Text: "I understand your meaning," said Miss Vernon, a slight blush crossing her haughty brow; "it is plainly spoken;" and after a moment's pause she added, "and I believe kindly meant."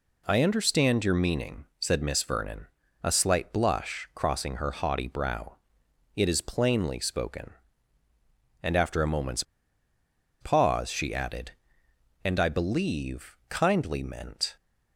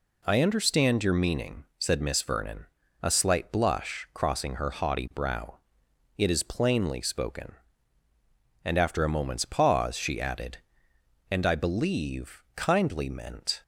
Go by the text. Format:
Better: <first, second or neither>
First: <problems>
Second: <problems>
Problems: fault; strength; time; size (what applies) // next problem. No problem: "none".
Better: second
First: pauses between "moment's" and "pause"; noticeable; at 9.4 s; 0.98 s long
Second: none